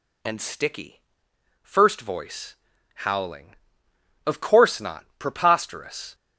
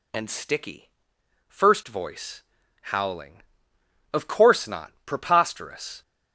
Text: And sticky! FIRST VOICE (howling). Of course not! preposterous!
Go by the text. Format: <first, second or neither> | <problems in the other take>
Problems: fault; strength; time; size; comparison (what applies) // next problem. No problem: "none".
neither | none